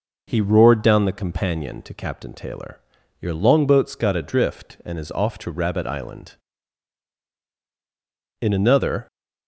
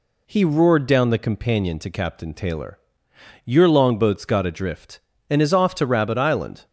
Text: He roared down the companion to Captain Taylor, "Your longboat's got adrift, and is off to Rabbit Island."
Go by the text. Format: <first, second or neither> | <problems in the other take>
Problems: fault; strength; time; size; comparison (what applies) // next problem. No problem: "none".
second | goes on to say "In another"; noticeable; from 8.3 s on; 0.68 s long